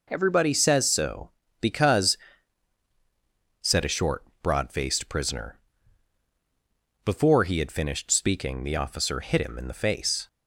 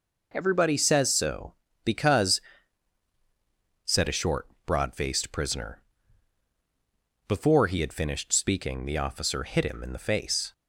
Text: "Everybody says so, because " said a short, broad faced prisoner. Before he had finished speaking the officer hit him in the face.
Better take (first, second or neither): neither